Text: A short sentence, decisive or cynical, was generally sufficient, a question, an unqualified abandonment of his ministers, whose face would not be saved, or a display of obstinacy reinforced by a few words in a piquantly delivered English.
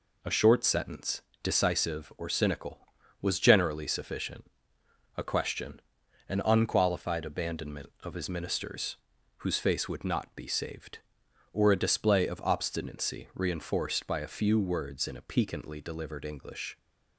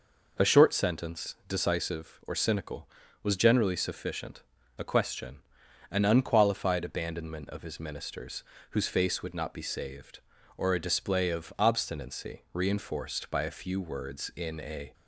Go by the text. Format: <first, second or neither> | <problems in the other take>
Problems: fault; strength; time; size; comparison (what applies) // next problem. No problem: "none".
first | stops before "piquantly delivered English"; at 14.9 s